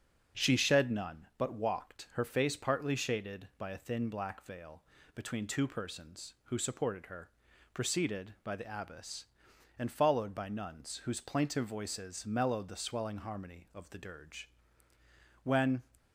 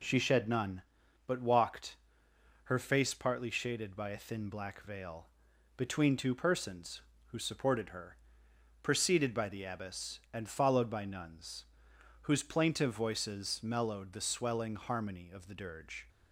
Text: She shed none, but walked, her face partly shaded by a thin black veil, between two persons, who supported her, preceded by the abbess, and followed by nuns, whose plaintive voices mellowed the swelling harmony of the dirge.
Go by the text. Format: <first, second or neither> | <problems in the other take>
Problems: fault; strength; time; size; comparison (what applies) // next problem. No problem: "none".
second | starts louder than the rest; until 1.4 s; 7 dB // goes on to say "When"; slight; from 15.4 s on; 0.40 s long